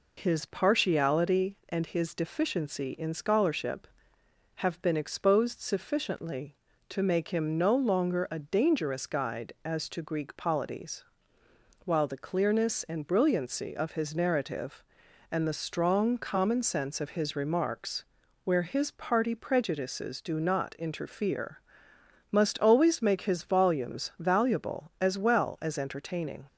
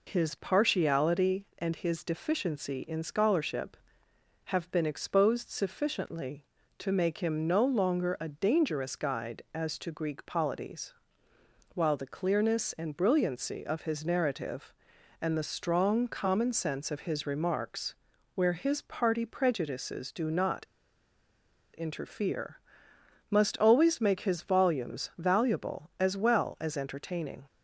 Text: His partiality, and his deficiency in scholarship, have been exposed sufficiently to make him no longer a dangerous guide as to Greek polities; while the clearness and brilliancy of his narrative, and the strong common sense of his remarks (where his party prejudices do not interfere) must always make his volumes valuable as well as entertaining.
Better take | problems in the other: first | pauses between "not" and "interfere"; at 20.6 s; 1.1 s long

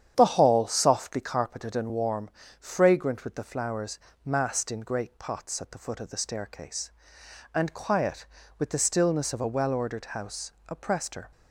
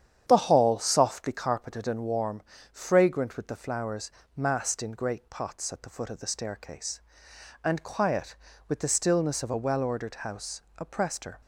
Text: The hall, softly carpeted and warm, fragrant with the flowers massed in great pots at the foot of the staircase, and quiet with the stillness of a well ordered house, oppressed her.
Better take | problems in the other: neither | starts louder than the rest; strong; the same in both // pauses between "flowers" and "massed"; slight; the same in both

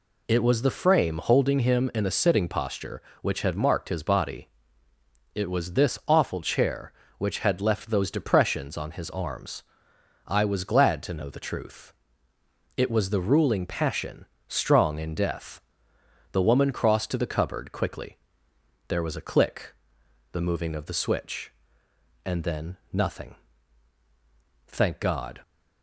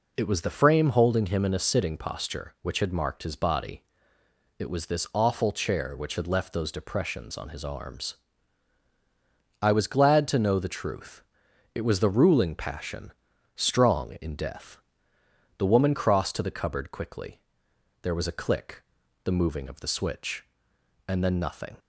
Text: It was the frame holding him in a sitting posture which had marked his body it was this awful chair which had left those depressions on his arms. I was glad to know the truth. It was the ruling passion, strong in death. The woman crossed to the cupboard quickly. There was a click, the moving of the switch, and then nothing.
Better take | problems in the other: second | pauses between "body" and "it"; noticeable; at 4.4 s; 0.86 s long; noticeable in the second // pauses between "then" and "nothing"; slight; at 22.7 s; 0.16 s long // goes on to say "Thank God"; noticeable; from 24.6 s on; 0.72 s long

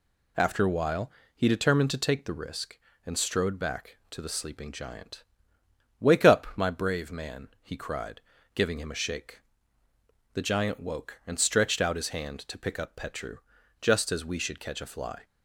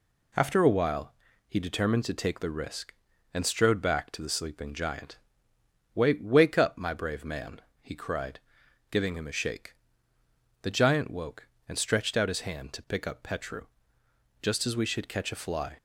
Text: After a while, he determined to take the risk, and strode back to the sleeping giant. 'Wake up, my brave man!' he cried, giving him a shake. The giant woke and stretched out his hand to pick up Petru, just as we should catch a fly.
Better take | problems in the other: first | says "Wake" twice; at 6.2 s

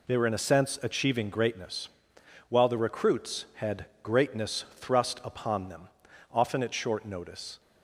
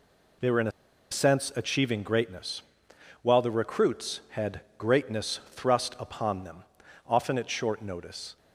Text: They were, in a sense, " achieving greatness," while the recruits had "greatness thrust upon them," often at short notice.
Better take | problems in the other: first | pauses between "a" and "sense"; at 0.7 s; 0.41 s long // pauses between "had" and "greatness"; slight; at 4.6 s; 0.18 s long; slight in the first

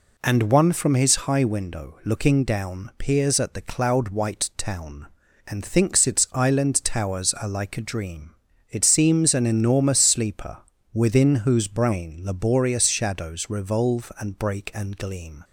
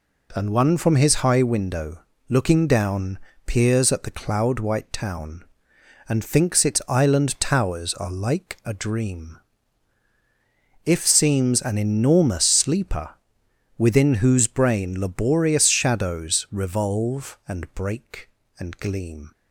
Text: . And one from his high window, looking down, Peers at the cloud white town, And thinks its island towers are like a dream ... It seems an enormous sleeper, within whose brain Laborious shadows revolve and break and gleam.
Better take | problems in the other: first | says "If" for "It"; at 10.8 s

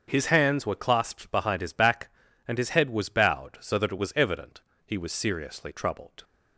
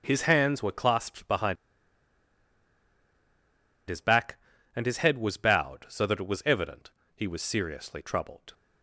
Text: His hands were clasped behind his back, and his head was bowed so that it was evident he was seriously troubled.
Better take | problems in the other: first | starts louder than the rest; until 1.0 s; 7 dB; also in the first // pauses between "behind" and "his"; strong; at 1.5 s; 2.3 s long // pauses between "evident" and "he"; slight; at 6.9 s; 0.24 s long; slight in the first

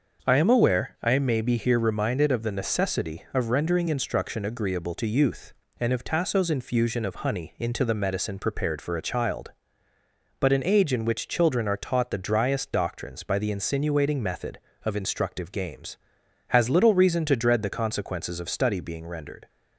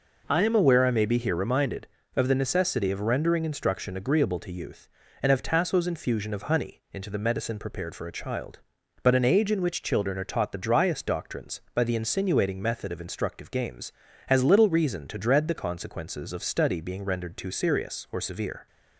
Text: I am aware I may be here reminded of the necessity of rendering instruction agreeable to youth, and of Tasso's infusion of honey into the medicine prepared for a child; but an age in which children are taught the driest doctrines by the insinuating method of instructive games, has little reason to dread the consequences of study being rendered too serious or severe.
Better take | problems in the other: second | starts louder than the rest; until 1.3 s; 6 dB // stops before "too serious or severe"; at 19.4 s

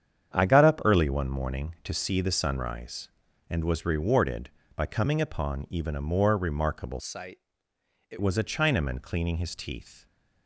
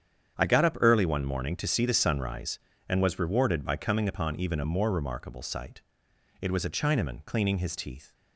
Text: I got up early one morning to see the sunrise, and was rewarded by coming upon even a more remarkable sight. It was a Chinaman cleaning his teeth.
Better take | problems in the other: second | starts louder than the rest; strong; until 1.3 s; 8.5 dB; strong in the second // changes voice from "sight" to "It"; from 6.9 to 8.1 s; 1.2 s long

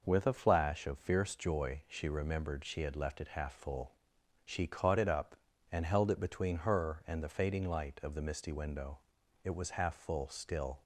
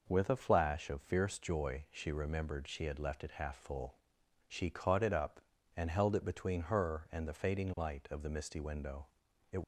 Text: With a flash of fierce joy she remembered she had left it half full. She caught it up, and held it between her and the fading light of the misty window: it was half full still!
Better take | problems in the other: first | stops before "was half full still"; at 9.6 s

